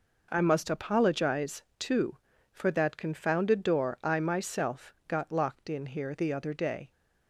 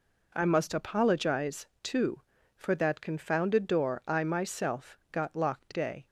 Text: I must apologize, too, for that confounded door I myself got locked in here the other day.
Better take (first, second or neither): first